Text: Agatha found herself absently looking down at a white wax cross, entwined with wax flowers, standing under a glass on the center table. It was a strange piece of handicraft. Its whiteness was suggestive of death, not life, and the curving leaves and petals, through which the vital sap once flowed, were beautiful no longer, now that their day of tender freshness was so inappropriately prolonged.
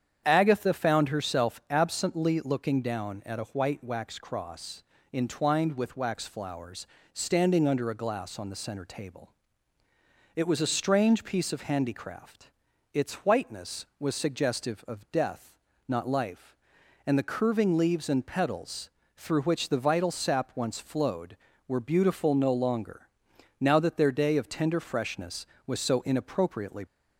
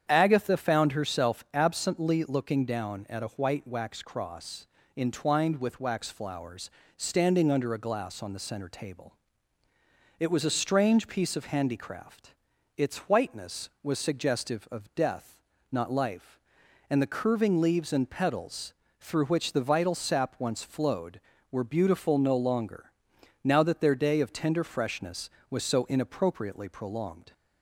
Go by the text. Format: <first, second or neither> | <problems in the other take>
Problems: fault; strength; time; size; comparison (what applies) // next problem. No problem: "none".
second | starts louder than the rest; strong; until 1.2 s; 8.5 dB; strong in the second // stops before "prolonged"; at 26.8 s